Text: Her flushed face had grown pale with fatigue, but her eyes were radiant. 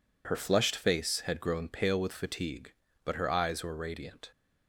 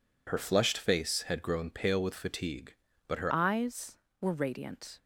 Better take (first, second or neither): first